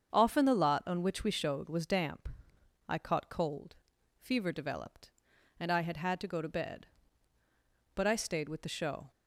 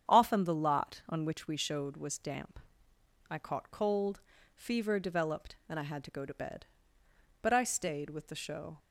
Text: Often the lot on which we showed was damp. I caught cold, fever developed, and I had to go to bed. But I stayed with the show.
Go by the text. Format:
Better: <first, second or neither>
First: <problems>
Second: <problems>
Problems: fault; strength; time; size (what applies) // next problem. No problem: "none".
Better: second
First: starts louder than the rest; until 1.1 s; 7 dB // says "had" twice; at 5.9 s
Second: starts louder than the rest; strong; until 1.1 s; 8 dB